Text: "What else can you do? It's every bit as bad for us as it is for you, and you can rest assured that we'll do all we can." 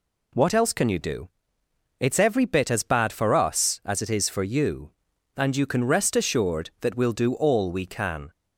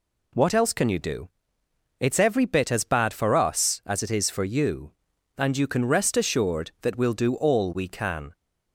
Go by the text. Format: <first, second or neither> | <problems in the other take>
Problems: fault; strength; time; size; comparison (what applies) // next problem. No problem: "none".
neither | none